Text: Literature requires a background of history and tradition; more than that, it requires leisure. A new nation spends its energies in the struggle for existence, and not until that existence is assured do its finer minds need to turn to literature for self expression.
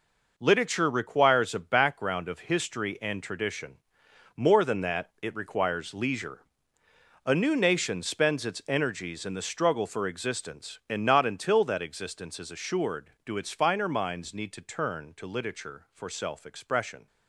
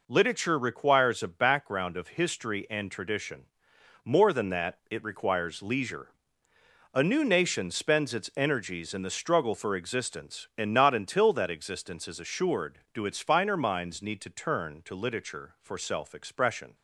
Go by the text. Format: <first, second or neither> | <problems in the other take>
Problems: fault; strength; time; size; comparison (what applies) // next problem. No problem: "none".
second | gets quieter; strong; throughout; 8 dB